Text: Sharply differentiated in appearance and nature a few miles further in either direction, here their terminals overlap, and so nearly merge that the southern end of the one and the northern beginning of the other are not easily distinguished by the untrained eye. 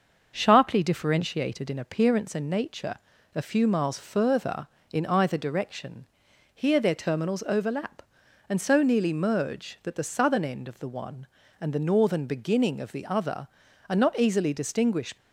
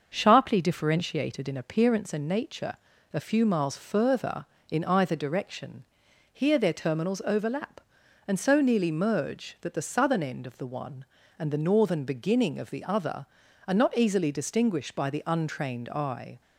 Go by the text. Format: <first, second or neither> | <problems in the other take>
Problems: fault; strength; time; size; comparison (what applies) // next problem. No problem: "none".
second | starts louder than the rest; until 1.3 s; 6.5 dB; also in the second // pauses between "nature" and "a"; at 2.9 s; 0.40 s long; also in the second // stops before "by the untrained eye"; at 15.1 s